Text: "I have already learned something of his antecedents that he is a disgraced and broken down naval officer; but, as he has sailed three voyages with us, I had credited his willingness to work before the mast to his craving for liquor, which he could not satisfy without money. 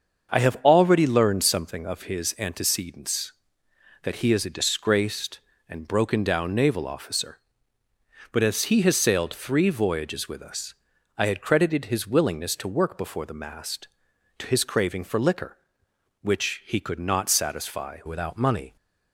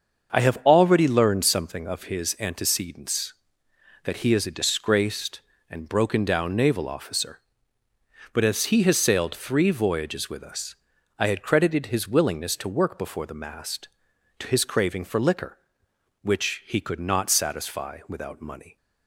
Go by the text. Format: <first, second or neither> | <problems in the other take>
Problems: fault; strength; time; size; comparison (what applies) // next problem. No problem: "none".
second | starts louder than the rest; until 1.4 s; 6.5 dB; also in the second // changes voice at "without"; from 18.0 s on; 0.7 s long